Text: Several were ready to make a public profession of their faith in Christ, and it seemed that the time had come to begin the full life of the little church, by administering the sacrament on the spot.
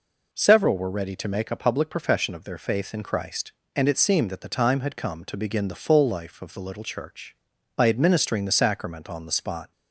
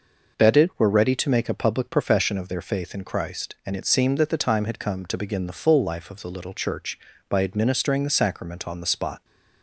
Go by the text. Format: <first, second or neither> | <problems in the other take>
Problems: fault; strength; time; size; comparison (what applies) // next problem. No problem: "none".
first | says "Bedded" for "Several"; at 0.3 s